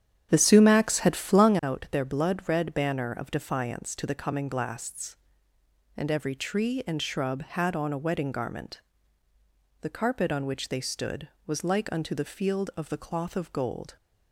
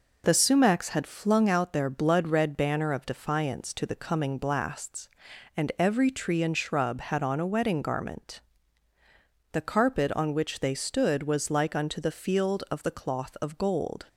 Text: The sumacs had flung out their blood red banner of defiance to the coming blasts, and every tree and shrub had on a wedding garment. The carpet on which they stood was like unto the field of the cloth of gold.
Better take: second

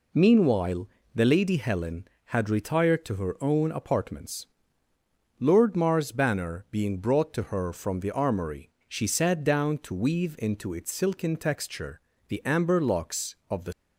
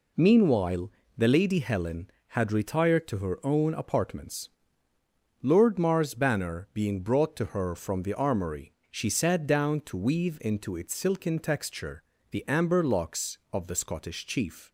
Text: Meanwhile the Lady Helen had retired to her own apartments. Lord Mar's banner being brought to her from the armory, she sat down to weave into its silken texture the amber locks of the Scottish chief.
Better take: second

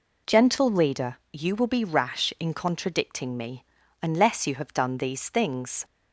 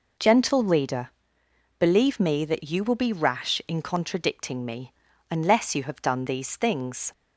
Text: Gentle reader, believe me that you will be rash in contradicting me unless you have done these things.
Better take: second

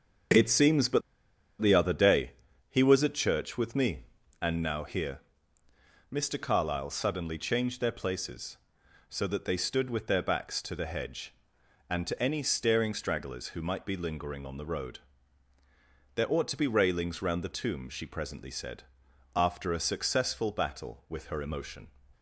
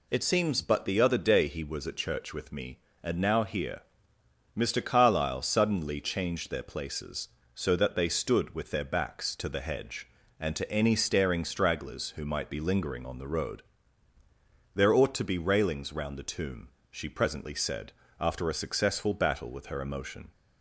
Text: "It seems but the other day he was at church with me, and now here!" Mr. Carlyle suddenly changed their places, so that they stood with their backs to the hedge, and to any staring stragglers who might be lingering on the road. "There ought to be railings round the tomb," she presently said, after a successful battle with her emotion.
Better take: second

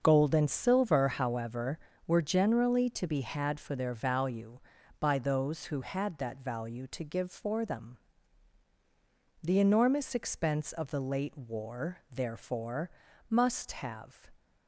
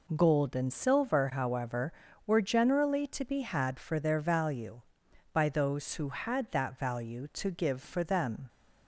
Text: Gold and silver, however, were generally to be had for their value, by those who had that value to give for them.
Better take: second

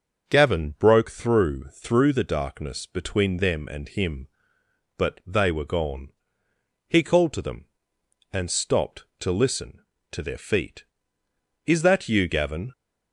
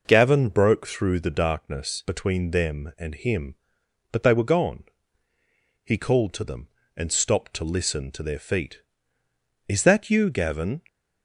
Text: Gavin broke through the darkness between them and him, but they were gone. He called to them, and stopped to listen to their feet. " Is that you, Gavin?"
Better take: second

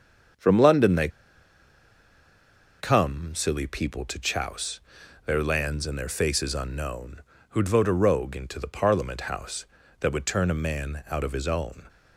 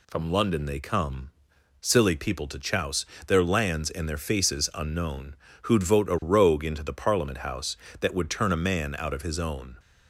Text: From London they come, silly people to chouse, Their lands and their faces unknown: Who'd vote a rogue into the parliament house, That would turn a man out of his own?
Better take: second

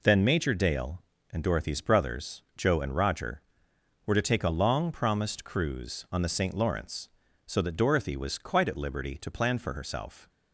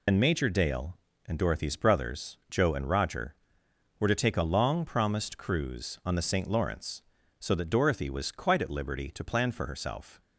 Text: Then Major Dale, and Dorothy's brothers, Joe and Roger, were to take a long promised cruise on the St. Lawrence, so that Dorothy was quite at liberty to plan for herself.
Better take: first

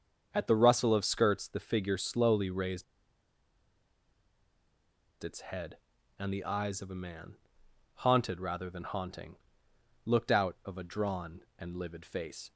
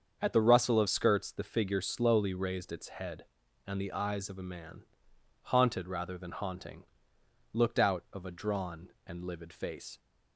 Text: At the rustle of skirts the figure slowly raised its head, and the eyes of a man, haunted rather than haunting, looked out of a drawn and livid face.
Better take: second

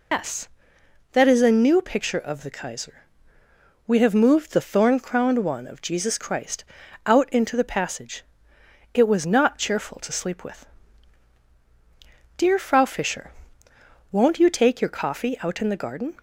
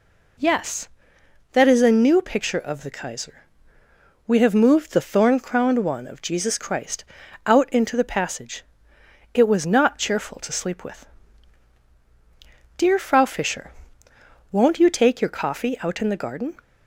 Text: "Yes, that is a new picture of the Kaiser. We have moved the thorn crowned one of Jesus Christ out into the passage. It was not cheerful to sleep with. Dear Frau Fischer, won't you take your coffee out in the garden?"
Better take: second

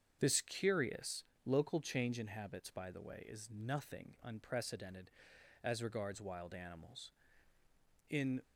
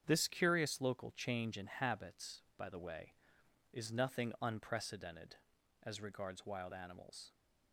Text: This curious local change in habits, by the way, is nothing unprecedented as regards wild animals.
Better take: second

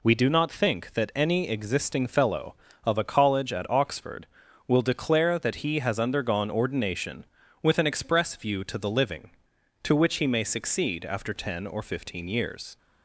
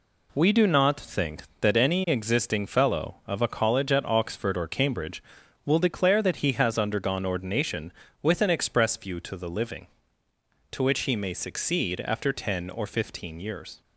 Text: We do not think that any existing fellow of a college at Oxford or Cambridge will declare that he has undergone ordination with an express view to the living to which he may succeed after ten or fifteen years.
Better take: second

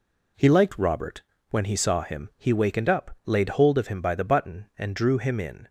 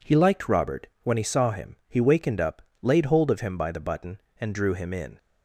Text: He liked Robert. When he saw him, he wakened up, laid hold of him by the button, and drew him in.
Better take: neither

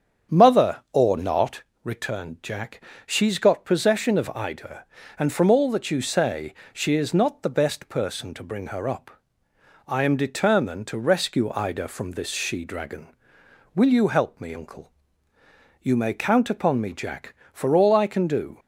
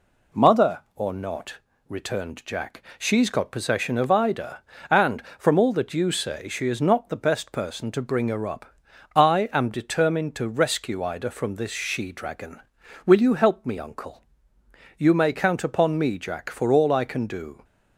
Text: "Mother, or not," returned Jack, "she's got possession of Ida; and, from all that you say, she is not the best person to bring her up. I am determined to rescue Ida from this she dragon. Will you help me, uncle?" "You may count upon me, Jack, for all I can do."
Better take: second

